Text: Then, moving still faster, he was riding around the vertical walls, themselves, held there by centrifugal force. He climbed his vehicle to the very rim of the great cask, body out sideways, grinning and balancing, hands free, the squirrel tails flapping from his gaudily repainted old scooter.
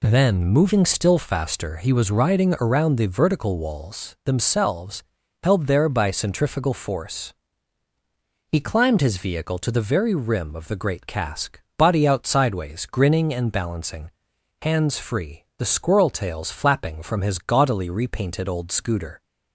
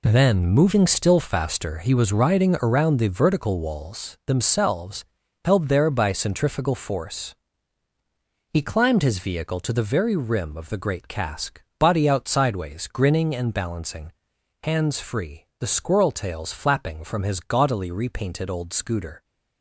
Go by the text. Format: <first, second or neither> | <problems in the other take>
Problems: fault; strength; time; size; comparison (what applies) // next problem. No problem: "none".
first | gets quieter; strong; throughout; 10 dB